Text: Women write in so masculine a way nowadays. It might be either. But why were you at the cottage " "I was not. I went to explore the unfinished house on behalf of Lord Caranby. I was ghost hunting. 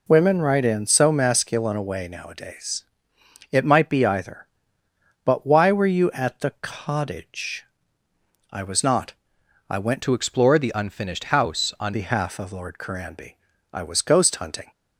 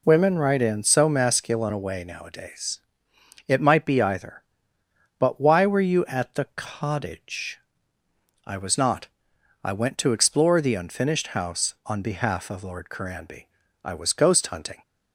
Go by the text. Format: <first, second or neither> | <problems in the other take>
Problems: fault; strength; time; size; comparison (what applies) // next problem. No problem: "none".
second | changes voice from "to" to "on"; from 10.0 to 11.9 s; 1.9 s long